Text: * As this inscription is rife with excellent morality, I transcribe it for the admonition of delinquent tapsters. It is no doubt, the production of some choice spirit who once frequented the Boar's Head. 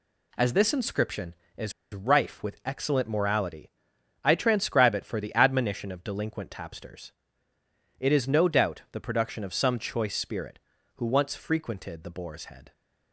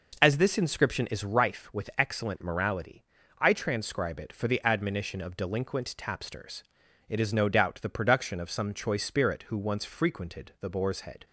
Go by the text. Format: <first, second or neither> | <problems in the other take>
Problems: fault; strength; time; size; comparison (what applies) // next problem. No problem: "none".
second | pauses between "is" and "rife"; slight; at 1.7 s; 0.21 s long